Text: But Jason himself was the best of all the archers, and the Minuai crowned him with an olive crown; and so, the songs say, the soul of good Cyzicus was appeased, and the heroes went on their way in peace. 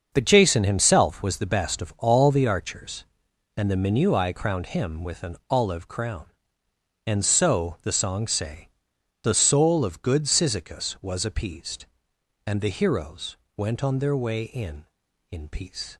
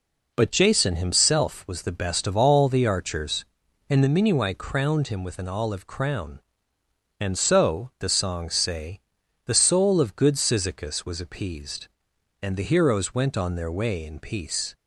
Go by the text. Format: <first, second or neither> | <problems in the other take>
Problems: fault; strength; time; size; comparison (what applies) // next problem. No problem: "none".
second | starts louder than the rest; until 1.1 s; 6.5 dB // pauses between "heroes" and "went"; slight; at 13.3 s; 0.20 s long // says "in" twice; at 15.3 s